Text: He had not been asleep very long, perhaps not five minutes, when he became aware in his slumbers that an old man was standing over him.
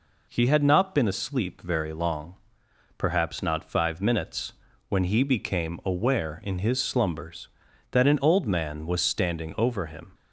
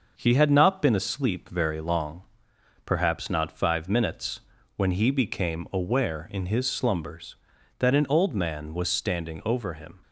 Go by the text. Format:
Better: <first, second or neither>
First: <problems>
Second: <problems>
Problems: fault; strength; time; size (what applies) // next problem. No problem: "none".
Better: first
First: none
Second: gets quieter; throughout; 3.5 dB